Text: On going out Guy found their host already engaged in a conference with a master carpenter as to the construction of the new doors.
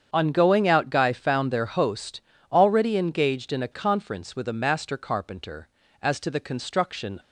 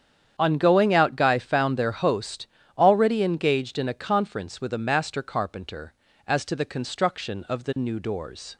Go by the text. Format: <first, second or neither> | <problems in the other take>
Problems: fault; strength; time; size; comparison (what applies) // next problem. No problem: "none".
second | starts louder than the rest; strong; until 1.1 s; 7.5 dB; strong in the second // pauses between "host" and "already"; slight; at 2.1 s; 0.32 s long; slight in the second // stops before "of the new doors"; at 7.2 s